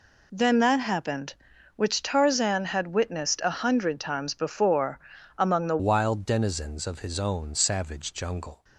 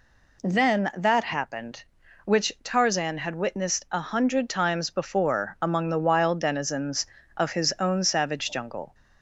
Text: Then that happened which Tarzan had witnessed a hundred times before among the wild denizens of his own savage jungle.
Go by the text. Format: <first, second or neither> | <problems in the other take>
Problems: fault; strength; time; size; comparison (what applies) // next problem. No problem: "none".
second | pauses between "before" and "among"; at 4.9 s; 0.40 s long // changes voice at "wild"; from 5.7 s on; 2.9 s long